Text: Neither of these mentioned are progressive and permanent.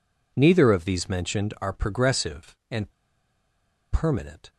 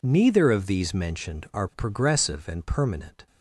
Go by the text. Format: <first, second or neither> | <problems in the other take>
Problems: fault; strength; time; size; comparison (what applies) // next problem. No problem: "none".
second | pauses between "and" and "permanent"; at 2.8 s; 1.0 s long